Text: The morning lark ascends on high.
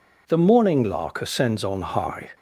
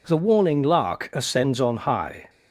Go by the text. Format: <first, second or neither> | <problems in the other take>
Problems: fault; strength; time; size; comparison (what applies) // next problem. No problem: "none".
first | says "warning" for "morning"; at 0.1 s